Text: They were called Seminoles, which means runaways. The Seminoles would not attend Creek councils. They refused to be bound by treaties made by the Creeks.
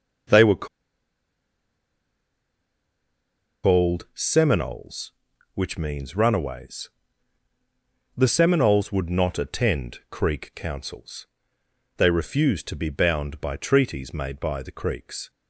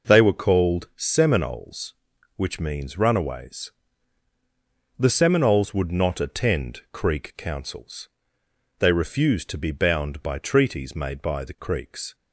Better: second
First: pauses between "were" and "called"; strong; at 0.6 s; 2.9 s long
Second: none

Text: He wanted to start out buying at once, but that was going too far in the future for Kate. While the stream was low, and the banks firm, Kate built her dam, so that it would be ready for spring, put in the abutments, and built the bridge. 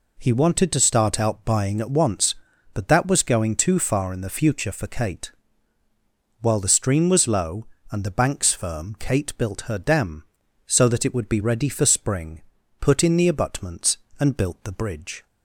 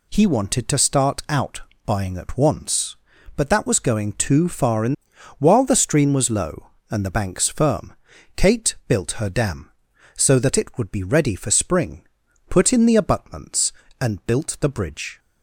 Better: first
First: none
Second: pauses between "out" and "buying"; slight; at 1.6 s; 0.24 s long // skips "the future for Kate"; at 5.1 s

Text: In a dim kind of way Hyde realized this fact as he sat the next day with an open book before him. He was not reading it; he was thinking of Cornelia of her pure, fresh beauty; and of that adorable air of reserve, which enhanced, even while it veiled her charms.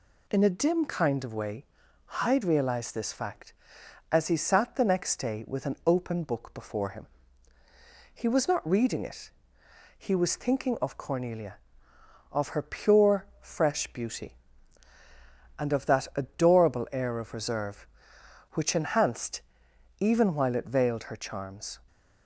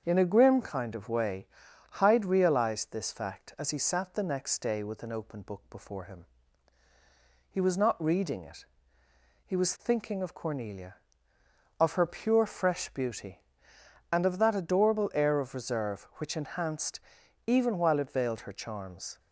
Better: first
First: pauses between "way" and "Hyde"; noticeable; at 1.6 s; 0.56 s long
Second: starts louder than the rest; until 1.0 s; 7 dB // says "grim" for "dim"; at 0.2 s // pauses between "way" and "Hyde"; noticeable; at 1.4 s; 0.46 s long

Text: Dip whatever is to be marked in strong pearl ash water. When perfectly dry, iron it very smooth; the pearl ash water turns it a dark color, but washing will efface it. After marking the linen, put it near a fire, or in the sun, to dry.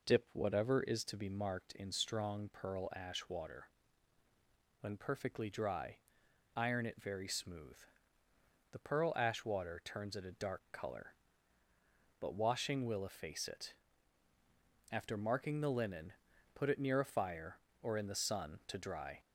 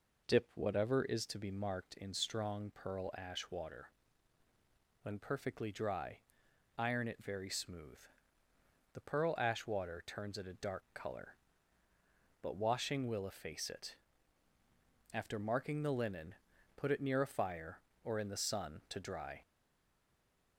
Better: first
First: none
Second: stays silent after the last word; from 19.4 s on; 1.1 s long

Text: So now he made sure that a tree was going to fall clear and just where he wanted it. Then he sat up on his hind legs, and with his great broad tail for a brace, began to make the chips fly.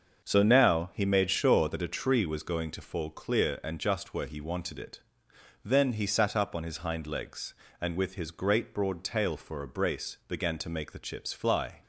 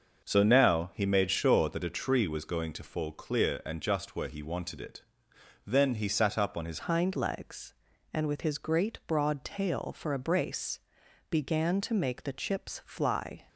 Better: first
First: starts louder than the rest; until 1.2 s; 6.5 dB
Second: starts louder than the rest; noticeable; until 1.2 s; 6 dB // changes voice at "hind"; from 6.8 s on; 6.6 s long

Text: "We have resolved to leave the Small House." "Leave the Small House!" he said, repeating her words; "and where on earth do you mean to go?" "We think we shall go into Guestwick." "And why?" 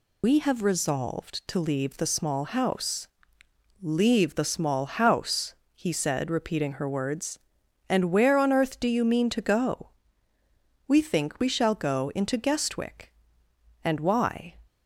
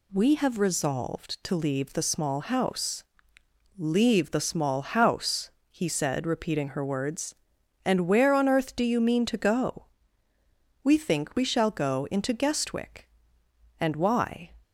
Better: second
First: loses the start of "We"; at 0.2 s; 85 ms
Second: none

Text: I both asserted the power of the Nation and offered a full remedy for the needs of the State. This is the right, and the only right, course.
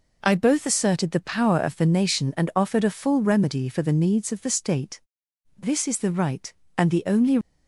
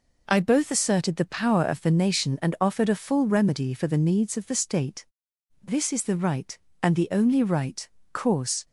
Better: second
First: stops before "right course"; at 7.4 s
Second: none

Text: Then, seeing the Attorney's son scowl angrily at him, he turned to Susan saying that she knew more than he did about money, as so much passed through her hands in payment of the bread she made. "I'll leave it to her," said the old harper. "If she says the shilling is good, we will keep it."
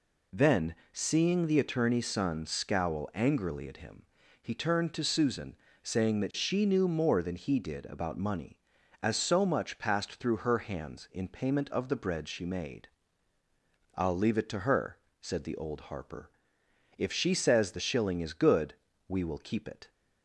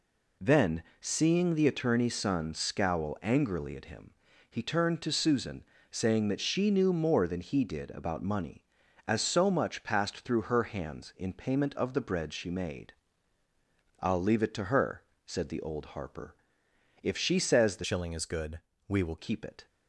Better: first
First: pauses between "Susan" and "saying"; slight; at 5.5 s; 0.26 s long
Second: pauses between "Susan" and "saying"; slight; at 5.6 s; 0.26 s long // changes voice from "shilling" to "will"; from 17.8 to 19.1 s; 1.3 s long

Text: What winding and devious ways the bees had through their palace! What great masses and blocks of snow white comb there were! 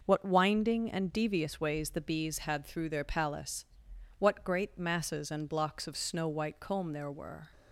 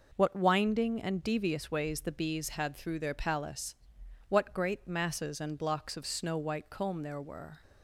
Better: neither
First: none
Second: none

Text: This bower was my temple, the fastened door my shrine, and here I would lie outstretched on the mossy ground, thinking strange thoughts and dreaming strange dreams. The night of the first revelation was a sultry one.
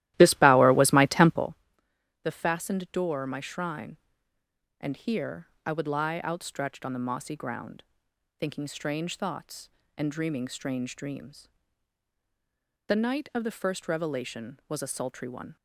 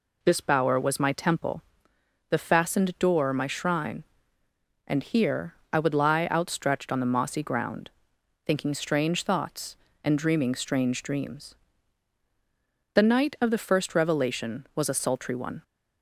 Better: second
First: starts louder than the rest; strong; until 1.6 s; 15 dB // pauses between "here" and "I"; slight; at 5.4 s; 0.18 s long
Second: pauses between "here" and "I"; slight; at 5.5 s; 0.18 s long

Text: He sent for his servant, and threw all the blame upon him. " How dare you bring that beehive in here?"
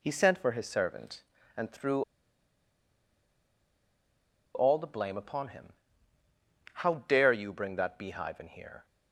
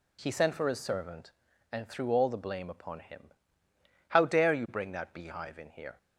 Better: second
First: pauses between "threw" and "all"; strong; at 2.0 s; 2.5 s long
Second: none

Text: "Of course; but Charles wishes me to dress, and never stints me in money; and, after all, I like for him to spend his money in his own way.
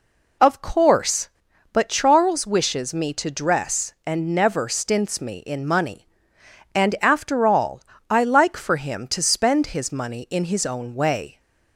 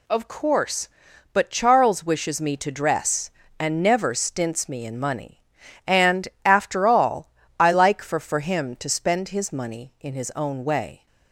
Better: first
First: none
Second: says "for" twice; at 8.1 s

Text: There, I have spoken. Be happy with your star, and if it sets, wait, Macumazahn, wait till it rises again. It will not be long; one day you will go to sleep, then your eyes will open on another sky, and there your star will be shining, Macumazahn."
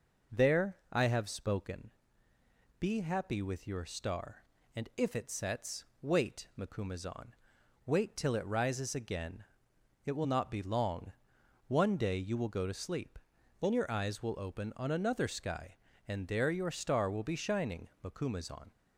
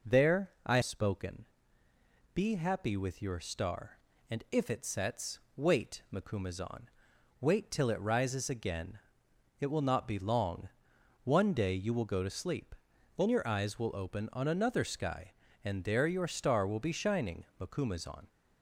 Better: first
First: none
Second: skips "have"; at 0.8 s

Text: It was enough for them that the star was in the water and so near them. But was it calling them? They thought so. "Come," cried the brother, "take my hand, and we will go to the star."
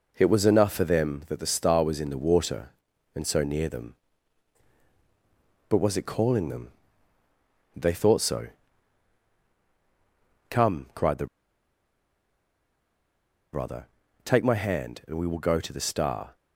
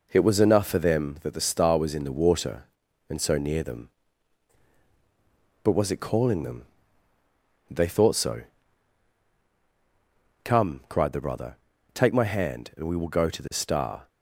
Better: second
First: pauses between "the" and "brother"; strong; at 11.2 s; 2.2 s long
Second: none

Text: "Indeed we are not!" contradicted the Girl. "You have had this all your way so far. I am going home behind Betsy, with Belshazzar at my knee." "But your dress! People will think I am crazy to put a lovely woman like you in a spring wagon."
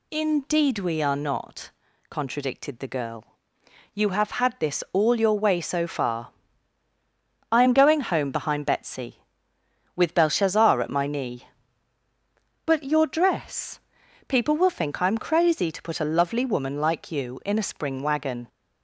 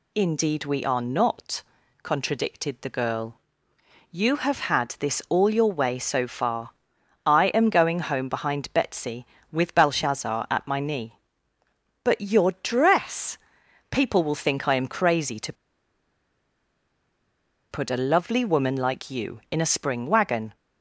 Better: first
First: none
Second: pauses between "to" and "put"; strong; at 15.5 s; 2.1 s long

